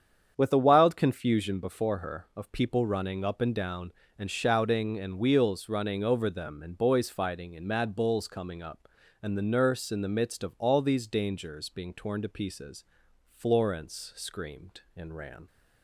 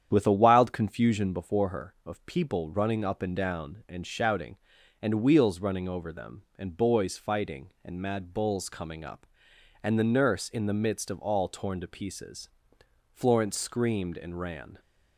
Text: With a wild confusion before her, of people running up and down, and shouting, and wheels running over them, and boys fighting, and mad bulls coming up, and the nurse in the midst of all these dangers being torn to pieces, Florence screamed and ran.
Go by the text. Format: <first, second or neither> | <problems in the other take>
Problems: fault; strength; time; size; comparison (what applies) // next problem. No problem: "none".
first | starts louder than the rest; strong; until 1.1 s; 9 dB; strong in the first // skips "these dangers being"; at 11.4 s